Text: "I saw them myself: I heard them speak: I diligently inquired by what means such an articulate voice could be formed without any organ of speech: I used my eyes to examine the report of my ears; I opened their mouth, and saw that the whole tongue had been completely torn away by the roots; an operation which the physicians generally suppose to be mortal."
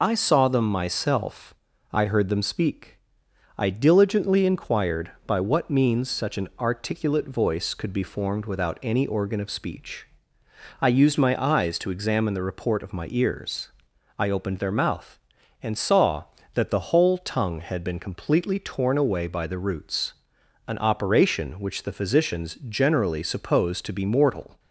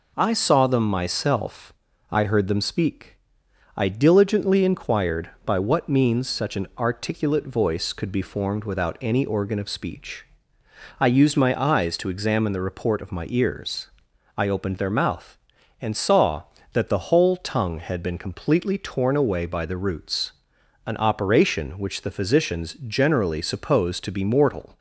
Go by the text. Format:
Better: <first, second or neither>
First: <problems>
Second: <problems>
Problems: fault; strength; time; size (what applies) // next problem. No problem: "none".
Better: second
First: loses the start of "I"; at 0.0 s; 35 ms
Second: none